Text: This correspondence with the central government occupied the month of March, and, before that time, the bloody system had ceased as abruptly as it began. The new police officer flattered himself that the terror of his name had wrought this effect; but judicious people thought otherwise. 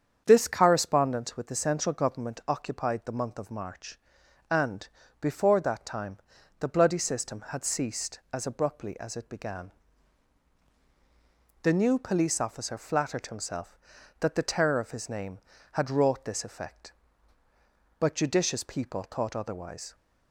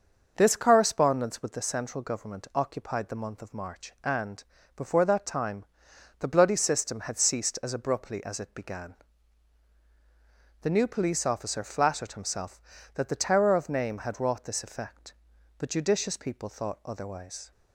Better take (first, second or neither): first